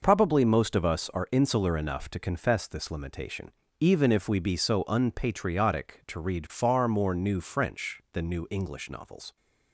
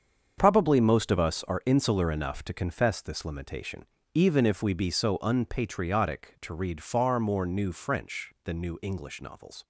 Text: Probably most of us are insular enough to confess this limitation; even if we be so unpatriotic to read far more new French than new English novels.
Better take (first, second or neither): first